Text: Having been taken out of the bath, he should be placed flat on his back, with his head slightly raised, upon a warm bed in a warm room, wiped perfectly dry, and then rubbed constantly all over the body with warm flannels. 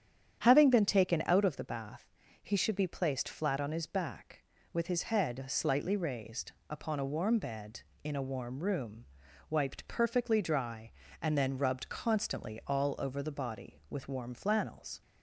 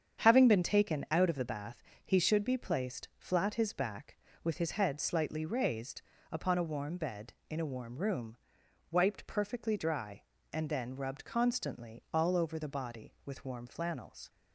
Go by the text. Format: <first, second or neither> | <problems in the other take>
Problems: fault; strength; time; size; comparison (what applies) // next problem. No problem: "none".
first | starts louder than the rest; strong; until 1.2 s; 8 dB; strong in the first // skips "on"; at 3.5 s